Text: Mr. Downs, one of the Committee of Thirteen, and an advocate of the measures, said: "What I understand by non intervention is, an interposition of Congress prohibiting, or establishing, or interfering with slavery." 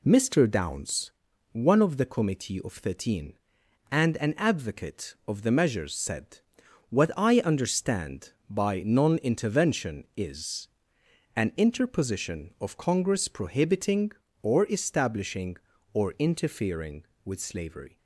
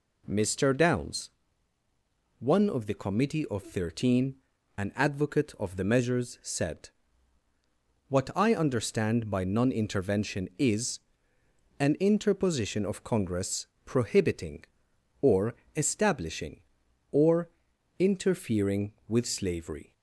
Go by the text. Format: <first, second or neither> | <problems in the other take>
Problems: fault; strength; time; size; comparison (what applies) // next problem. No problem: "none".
first | skips "and"; at 4.5 s // pauses between "Congress" and "prohibiting"; slight; at 13.6 s; 0.18 s long // pauses between "or" and "establishing"; slight; at 15.5 s; 0.24 s long // pauses between "or" and "interfering"; noticeable; at 17.5 s; 0.48 s long